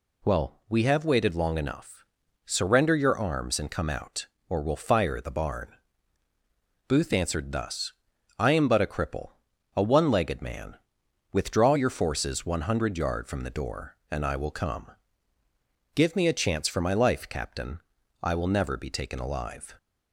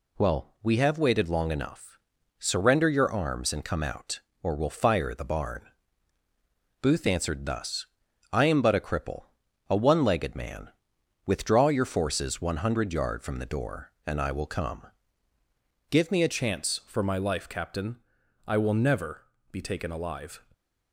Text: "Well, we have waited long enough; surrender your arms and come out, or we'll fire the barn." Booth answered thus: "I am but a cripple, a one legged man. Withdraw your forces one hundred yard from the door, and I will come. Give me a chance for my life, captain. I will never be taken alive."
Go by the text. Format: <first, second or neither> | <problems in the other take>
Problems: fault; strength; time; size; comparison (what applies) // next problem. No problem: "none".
first | changes voice at "chance"; from 16.3 s on; 4.1 s long // pauses between "never" and "be"; slight; at 19.2 s; 0.26 s long